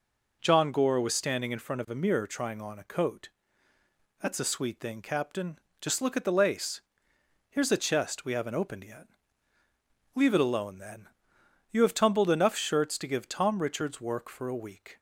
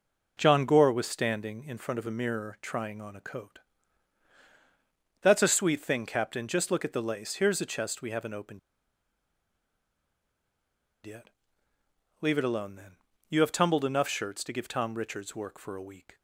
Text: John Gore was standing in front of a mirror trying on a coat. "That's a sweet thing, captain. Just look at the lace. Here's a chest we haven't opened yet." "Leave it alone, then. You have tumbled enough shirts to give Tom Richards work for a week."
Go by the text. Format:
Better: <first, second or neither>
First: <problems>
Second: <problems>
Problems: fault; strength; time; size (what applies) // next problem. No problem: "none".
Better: first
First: none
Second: pauses between "opened" and "yet"; strong; at 8.5 s; 2.4 s long